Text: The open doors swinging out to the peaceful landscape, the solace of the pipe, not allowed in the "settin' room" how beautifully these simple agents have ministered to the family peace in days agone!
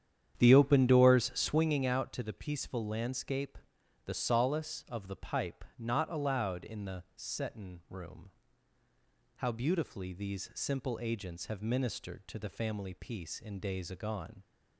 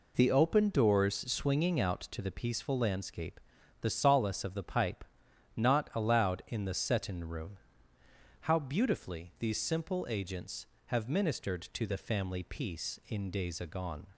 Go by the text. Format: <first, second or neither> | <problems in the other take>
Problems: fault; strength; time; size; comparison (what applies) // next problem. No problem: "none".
second | starts louder than the rest; strong; until 1.8 s; 9 dB // pauses between "room" and "how"; at 8.3 s; 1.0 s long; noticeable in the second